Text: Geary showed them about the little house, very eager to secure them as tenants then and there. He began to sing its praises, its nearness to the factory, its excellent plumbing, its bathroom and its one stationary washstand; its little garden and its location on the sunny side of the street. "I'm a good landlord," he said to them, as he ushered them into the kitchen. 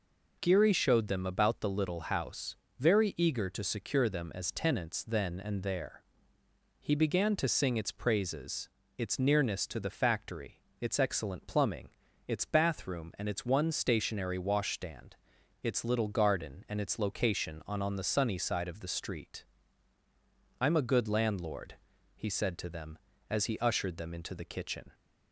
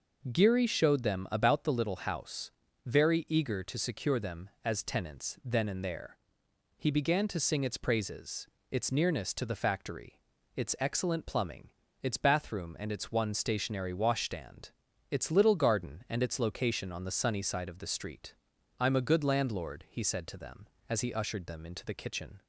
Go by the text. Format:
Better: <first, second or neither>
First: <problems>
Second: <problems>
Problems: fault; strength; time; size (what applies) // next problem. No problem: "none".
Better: second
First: says "on" twice; at 17.8 s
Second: none